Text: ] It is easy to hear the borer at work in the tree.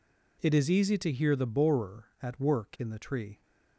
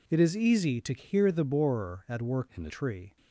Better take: first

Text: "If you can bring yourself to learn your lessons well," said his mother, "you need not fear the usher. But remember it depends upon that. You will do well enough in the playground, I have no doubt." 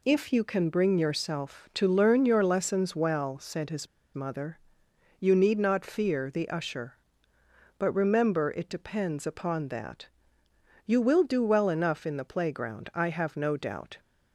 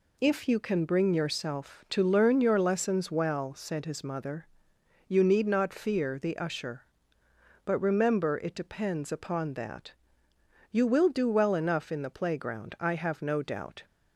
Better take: second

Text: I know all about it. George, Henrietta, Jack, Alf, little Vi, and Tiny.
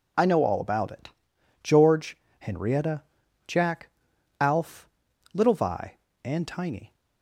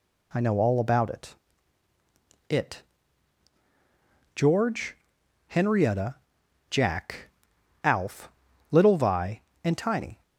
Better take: first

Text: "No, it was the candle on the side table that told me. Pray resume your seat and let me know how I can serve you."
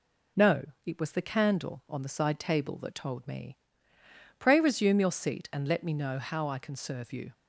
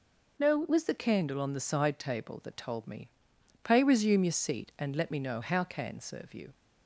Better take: first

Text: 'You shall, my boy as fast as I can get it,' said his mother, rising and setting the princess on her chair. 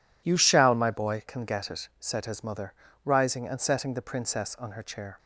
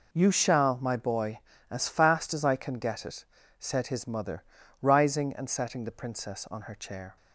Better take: second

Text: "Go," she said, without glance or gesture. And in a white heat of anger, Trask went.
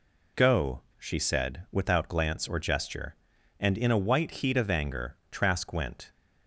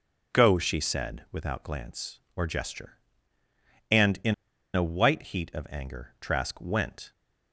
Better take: first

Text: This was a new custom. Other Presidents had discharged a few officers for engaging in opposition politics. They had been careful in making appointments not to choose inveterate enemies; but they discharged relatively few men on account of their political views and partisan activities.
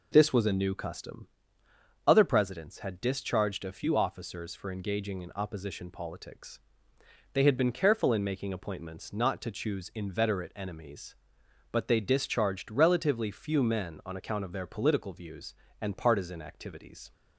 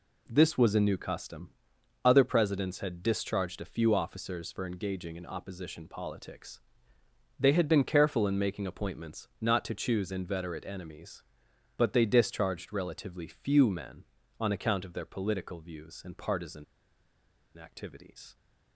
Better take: first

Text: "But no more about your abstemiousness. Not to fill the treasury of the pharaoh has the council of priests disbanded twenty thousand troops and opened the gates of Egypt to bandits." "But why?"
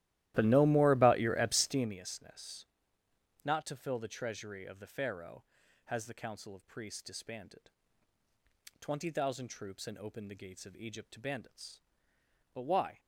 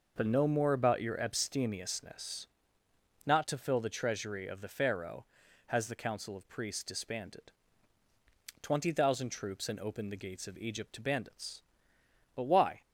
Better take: second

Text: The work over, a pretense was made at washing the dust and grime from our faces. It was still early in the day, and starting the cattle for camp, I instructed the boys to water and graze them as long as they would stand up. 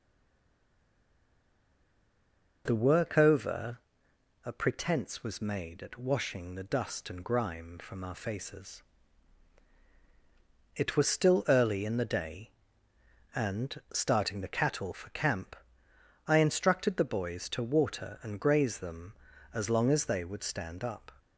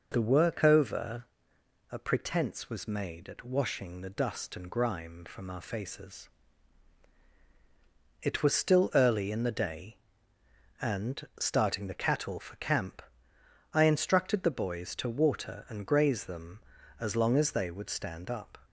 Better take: second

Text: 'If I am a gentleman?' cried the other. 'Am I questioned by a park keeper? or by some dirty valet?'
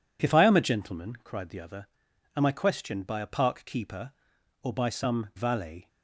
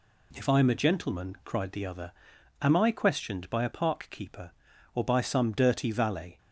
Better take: second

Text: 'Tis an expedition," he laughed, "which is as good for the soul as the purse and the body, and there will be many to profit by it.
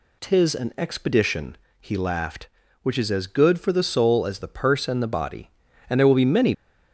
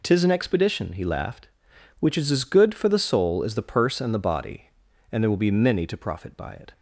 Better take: second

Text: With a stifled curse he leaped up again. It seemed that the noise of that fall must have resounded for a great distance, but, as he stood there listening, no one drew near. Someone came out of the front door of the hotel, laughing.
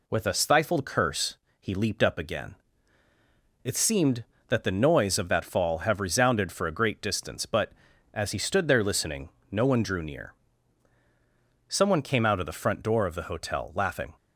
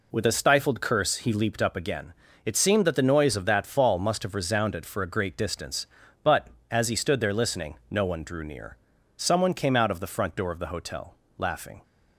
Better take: second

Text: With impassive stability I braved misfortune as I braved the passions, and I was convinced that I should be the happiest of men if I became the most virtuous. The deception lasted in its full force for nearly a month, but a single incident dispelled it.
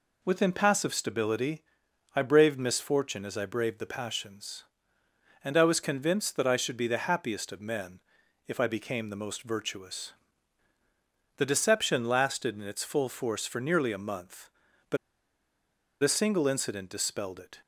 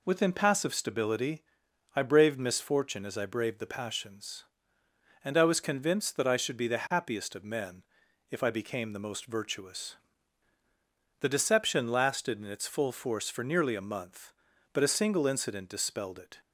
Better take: second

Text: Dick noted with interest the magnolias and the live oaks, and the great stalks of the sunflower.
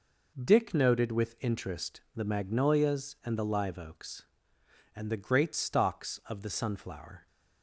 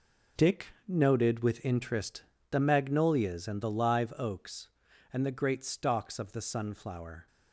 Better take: first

